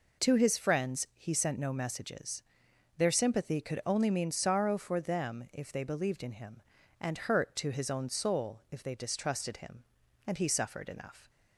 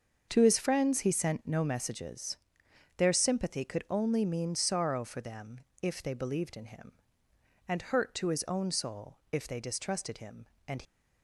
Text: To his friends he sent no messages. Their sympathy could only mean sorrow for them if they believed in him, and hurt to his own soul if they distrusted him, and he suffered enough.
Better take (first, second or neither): first